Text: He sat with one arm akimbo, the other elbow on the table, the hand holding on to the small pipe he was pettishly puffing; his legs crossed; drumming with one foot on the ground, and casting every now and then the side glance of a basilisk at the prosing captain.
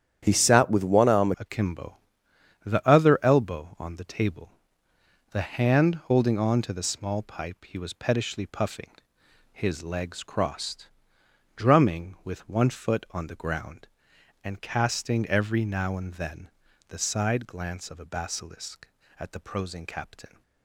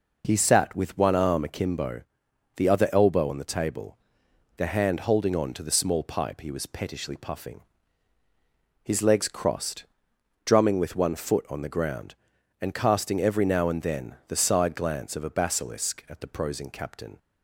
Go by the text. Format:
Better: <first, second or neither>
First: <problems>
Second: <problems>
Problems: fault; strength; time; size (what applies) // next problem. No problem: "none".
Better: second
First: starts louder than the rest; strong; until 1.2 s; 9.5 dB // changes voice at "akimbo"; from 1.3 s on; 19.1 s long // pauses between "then" and "the"; at 16.4 s; 0.38 s long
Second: none